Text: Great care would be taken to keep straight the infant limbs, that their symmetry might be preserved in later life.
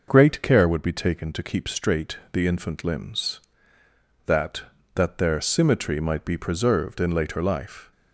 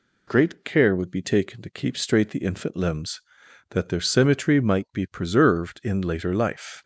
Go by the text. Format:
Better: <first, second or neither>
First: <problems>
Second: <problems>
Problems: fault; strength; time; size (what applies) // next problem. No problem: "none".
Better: second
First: pauses between "straight" and "the"; slight; at 2.1 s; 0.16 s long // says "that" twice; at 4.9 s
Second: none